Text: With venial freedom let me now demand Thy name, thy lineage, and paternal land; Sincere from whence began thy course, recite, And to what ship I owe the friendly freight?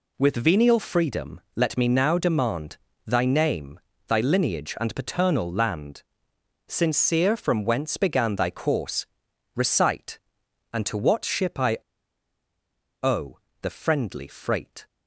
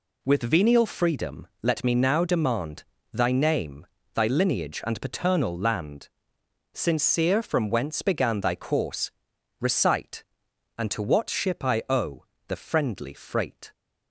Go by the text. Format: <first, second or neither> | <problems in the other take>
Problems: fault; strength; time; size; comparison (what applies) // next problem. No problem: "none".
second | pauses between "freedom" and "let"; slight; at 1.4 s; 0.16 s long; slight in the second // pauses between "demand" and "Thy"; slight; at 2.7 s; 0.28 s long; slight in the second // pauses between "I" and "owe"; at 11.7 s; 1.2 s long // pauses between "owe" and "the"; slight; at 13.3 s; 0.24 s long; slight in the second